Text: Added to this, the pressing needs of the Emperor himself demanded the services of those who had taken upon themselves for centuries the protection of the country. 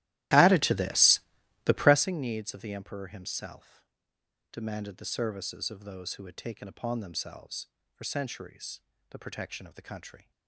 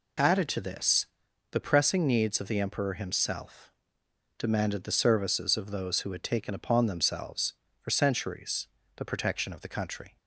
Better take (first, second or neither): second